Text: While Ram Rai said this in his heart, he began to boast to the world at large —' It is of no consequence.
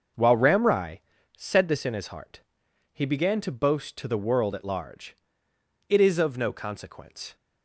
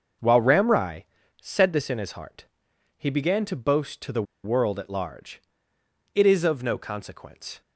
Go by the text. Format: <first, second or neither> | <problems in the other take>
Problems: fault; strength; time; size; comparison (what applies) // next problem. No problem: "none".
first | starts louder than the rest; noticeable; until 1.5 s; 6 dB; noticeable in the first // pauses between "Rai" and "said"; slight; at 1.0 s; 0.36 s long; slight in the first // pauses between "the" and "world"; slight; at 4.2 s; 0.21 s long